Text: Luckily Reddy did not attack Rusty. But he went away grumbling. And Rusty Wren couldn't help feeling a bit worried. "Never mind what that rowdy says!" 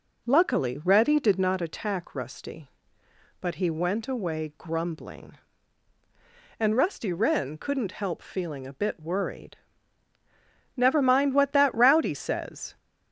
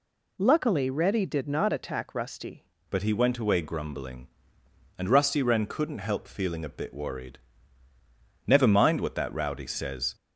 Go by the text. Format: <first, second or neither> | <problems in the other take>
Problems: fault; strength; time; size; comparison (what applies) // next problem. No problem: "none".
first | changes voice at "But"; from 2.8 s on; 7.3 s long